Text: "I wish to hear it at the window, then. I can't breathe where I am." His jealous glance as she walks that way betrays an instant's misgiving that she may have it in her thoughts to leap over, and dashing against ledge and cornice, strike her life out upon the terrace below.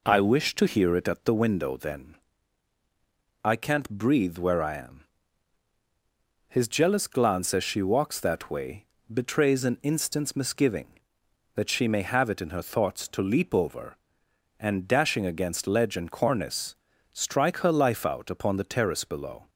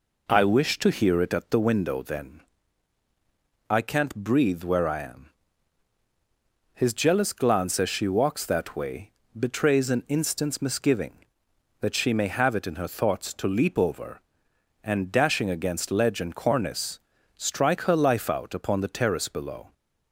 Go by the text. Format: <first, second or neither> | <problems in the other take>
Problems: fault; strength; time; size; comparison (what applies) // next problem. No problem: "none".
neither | pauses between "way" and "betrays"; slight; the same in both